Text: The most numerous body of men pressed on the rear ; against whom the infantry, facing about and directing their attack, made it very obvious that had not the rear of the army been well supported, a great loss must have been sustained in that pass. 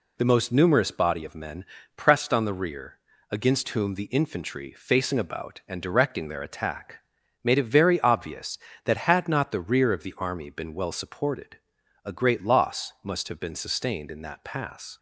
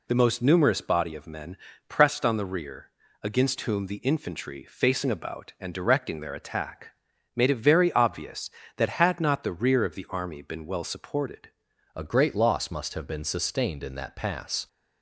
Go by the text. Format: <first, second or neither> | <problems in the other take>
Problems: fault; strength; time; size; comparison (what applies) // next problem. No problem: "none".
first | pauses between "men" and "pressed"; slight; at 1.5 s; 0.32 s long; slight in the first // changes voice at "a"; from 11.9 s on; 2.7 s long